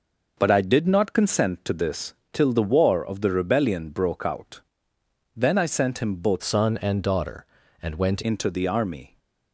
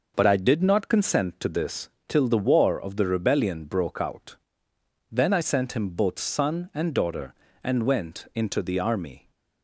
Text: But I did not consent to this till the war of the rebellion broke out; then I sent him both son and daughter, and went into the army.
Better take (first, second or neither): second